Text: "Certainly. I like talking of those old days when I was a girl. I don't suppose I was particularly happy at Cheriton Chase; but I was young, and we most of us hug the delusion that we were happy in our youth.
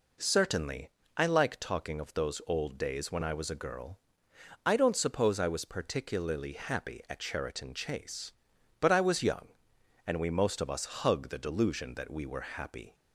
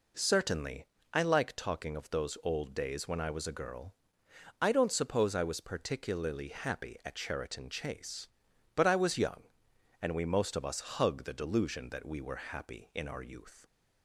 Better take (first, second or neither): second